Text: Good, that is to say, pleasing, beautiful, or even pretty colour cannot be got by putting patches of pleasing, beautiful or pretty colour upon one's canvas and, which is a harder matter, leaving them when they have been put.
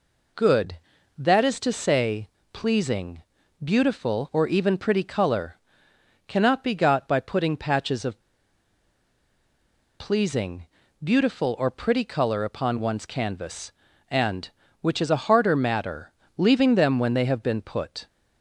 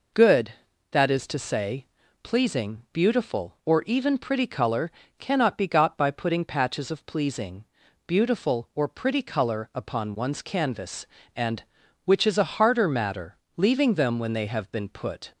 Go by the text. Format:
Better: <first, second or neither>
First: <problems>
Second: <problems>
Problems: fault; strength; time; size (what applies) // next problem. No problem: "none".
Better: second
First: pauses between "colour" and "cannot"; noticeable; at 5.5 s; 0.70 s long // pauses between "of" and "pleasing"; strong; at 8.1 s; 1.7 s long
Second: pauses between "colour" and "cannot"; slight; at 4.9 s; 0.28 s long